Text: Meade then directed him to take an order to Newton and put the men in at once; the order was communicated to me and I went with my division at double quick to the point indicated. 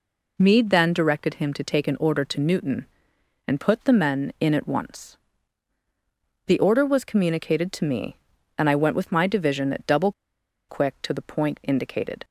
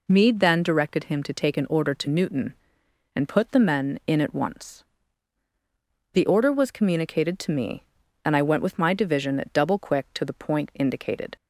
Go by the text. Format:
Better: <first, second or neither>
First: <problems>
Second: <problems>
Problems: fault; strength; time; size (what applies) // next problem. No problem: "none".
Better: second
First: pauses between "double" and "quick"; noticeable; at 10.1 s; 0.58 s long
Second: none